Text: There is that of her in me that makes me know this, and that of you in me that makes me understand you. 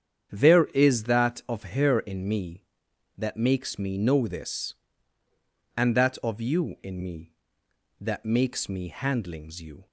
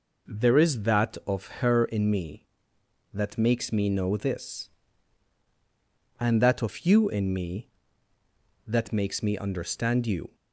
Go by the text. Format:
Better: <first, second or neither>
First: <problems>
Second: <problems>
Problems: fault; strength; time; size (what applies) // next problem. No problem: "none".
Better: second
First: starts louder than the rest; strong; until 1.4 s; 8.5 dB // says "handlings" for "understand"; at 8.8 s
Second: none